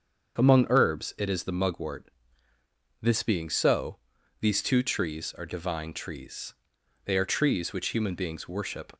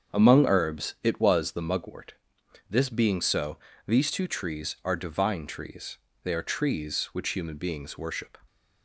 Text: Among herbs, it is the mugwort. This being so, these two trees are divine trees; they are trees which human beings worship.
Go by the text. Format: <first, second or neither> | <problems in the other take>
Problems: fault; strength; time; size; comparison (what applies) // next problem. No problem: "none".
first | starts louder than the rest; strong; until 1.1 s; 7 dB; also in the first // says "was" for "is"; at 1.2 s